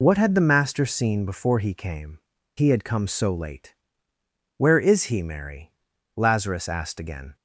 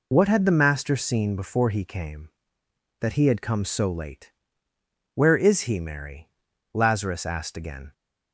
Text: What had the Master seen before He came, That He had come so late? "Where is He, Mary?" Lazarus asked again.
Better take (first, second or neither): second